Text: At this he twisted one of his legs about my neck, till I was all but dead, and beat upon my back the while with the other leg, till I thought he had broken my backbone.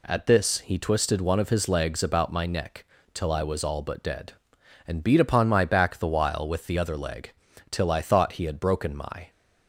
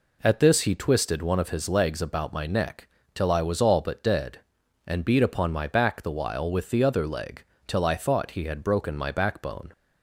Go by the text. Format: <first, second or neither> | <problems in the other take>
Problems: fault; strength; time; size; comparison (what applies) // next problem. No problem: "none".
second | stops before "backbone"; at 9.2 s